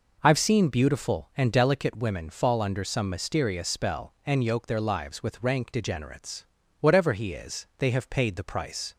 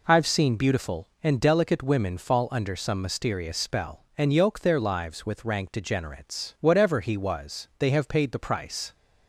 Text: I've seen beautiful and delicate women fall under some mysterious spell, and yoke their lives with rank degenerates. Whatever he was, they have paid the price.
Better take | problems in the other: second | says "is" for "was"; at 7.3 s

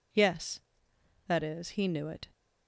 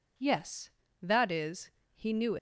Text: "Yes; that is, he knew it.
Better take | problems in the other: first | stops before "it"; at 2.3 s

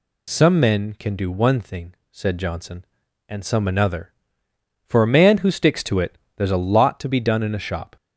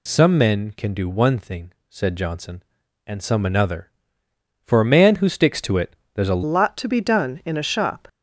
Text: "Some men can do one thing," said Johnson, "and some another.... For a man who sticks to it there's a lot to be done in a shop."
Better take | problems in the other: first | pauses between "it" and "there's"; slight; at 5.9 s; 0.18 s long; slight in the first // changes voice at "lot"; from 6.4 s on; 1.6 s long

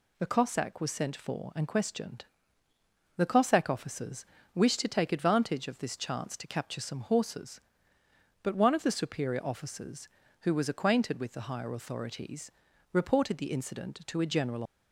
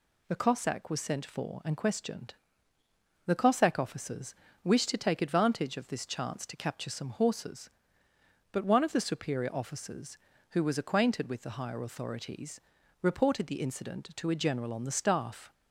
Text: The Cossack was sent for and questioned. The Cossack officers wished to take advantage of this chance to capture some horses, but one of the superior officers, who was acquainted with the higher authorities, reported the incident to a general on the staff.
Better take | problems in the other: second | pauses between "officers" and "wished"; slight; at 4.2 s; 0.30 s long; slight in the second // stops before "on the staff"; at 14.6 s

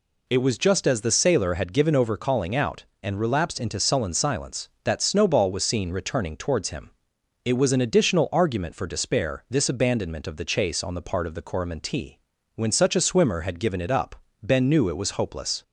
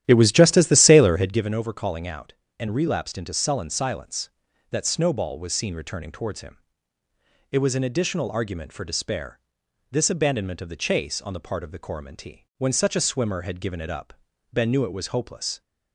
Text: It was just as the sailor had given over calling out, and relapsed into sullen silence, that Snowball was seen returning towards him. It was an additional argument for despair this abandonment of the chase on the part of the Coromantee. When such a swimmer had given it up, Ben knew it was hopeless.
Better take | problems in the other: first | starts louder than the rest; strong; until 1.5 s; 11.5 dB // pauses between "despair" and "this"; noticeable; at 9.3 s; 0.52 s long

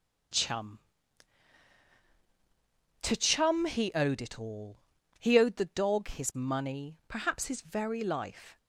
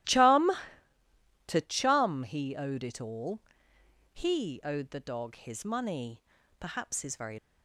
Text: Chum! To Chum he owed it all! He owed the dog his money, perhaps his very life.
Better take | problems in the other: first | starts louder than the rest; strong; until 2.0 s; 14.5 dB; strong in the first // stops before "life"; at 7.3 s

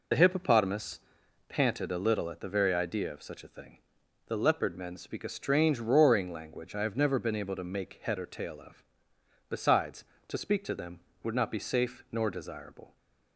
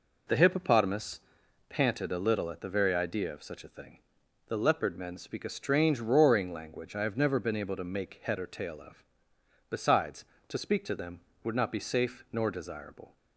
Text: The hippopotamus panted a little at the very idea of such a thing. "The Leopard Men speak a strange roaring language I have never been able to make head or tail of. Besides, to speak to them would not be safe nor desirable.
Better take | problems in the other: second | loses the start of "The"; at 0.1 s; 40 ms // pauses between "hippopotamus" and "panted"; noticeable; at 0.9 s; 0.50 s long; noticeable in the second

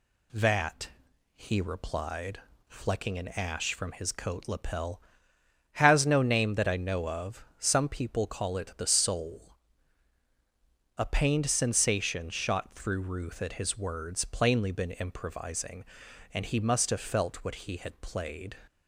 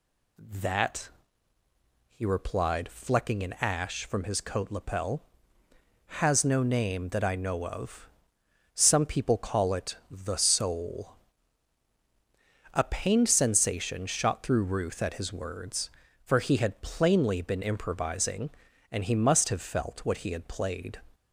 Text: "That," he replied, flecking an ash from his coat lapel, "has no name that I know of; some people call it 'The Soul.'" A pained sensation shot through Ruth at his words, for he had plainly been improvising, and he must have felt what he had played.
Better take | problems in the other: second | skips "for he had"; at 14.2 s

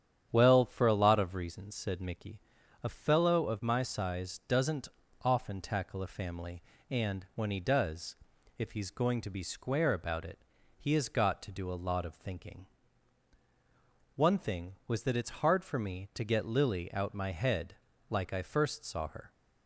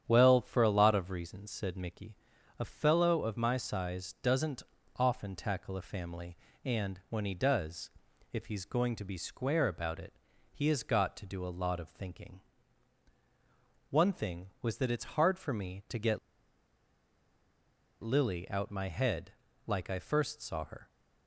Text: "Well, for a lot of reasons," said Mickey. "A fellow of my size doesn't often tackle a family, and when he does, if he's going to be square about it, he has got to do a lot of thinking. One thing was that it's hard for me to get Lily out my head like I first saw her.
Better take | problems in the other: first | starts louder than the rest; strong; until 1.0 s; 9 dB; strong in the first // pauses between "doesn't" and "often"; slight; at 4.6 s; 0.36 s long; slight in the first // pauses between "get" and "Lily"; strong; at 16.1 s; 1.8 s long // pauses between "head" and "like"; slight; at 19.3 s; 0.34 s long; slight in the first

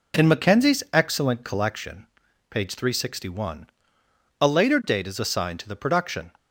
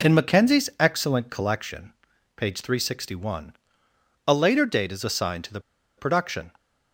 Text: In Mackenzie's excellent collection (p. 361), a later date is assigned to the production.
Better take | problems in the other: first | pauses between "the" and "production"; at 5.5 s; 0.37 s long

